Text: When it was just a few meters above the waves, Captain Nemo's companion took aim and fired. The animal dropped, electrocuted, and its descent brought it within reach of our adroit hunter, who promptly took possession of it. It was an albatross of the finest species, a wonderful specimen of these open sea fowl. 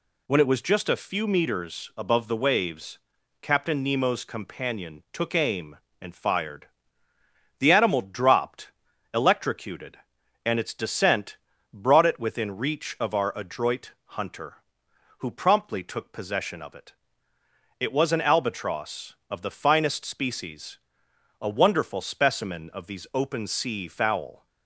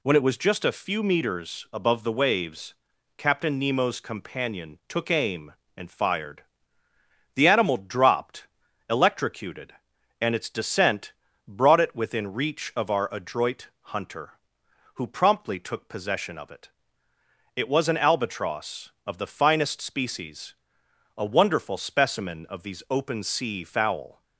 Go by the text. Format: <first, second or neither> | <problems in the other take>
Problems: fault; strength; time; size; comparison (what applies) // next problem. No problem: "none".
neither | pauses between "descent" and "brought"; slight; the same in both